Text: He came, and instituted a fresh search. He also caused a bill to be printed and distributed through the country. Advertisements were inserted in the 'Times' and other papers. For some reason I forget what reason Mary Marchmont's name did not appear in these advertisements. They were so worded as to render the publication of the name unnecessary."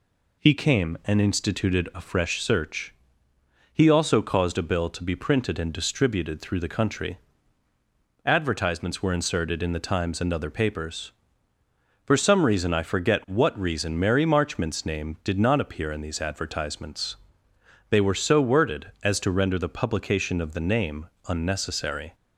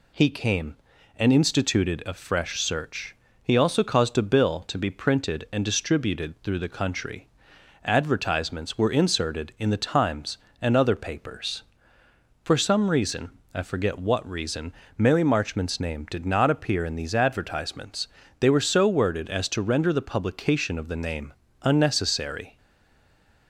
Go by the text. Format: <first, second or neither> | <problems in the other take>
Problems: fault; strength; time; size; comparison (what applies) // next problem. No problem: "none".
first | pauses between "reason" and "I"; slight; at 13.3 s; 0.24 s long // pauses between "reason" and "Mary"; slight; at 14.7 s; 0.24 s long // pauses between "name" and "unnecessary"; slight; at 21.3 s; 0.30 s long; slight in the first // stays silent after the last word; from 22.5 s on; 0.9 s long